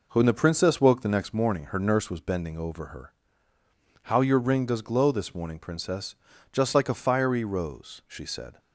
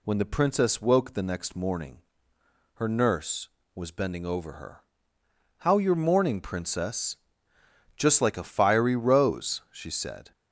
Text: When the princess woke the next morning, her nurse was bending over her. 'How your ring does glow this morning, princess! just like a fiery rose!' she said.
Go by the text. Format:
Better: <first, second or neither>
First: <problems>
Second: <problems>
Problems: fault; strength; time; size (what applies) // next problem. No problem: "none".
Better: first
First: none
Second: skips "ring does glow this"; at 5.9 s